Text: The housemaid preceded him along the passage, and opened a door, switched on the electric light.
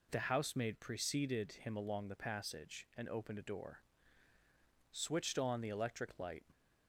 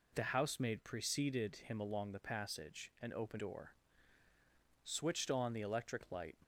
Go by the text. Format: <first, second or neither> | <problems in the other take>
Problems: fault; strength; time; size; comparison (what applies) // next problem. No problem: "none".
first | skips "a"; at 3.3 s